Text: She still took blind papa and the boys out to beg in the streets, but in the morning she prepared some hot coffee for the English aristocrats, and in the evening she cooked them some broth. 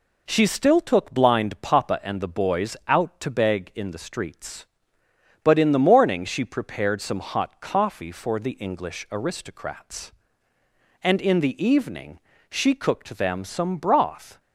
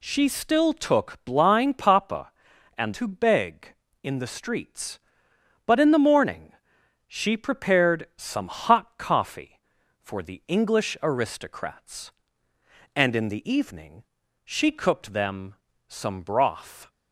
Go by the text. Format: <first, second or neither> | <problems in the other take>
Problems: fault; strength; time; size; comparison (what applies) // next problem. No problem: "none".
first | skips "the boys out"; at 2.9 s // pauses between "morning" and "she"; noticeable; at 6.5 s; 0.54 s long // pauses between "evening" and "she"; at 14.0 s; 0.38 s long; slight in the first // pauses between "them" and "some"; slight; at 15.5 s; 0.34 s long